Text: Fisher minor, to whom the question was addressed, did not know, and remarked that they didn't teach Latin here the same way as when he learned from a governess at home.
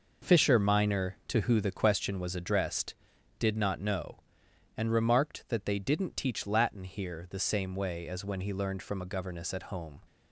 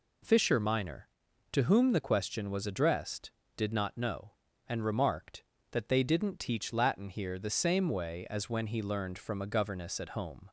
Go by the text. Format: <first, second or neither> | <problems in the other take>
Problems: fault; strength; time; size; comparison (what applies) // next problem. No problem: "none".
second | says "who" for "whom"; at 1.4 s